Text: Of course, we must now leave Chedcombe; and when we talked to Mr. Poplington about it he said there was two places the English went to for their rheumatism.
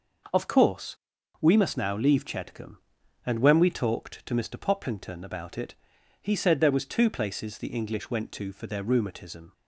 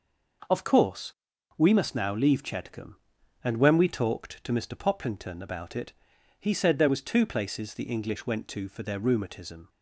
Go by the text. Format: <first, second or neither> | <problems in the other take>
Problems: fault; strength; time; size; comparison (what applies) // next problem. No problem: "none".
neither | pauses between "it" and "he"; noticeable; the same in both